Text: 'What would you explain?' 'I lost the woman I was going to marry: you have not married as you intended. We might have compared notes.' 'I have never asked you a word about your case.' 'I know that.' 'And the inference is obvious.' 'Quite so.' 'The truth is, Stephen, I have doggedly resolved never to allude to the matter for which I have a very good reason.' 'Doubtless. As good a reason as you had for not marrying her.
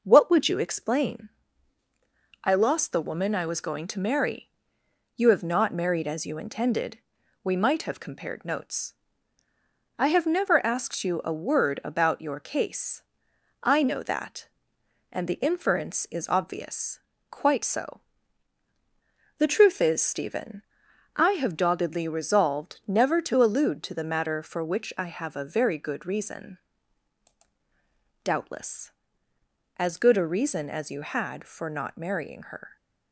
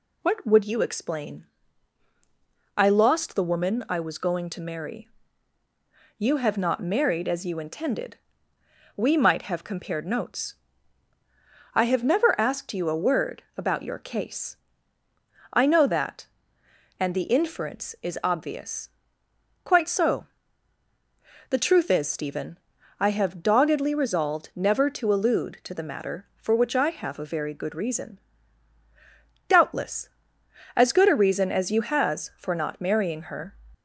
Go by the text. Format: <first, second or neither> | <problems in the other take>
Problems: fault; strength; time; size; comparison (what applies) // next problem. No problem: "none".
first | says "has" for "had"; at 31.8 s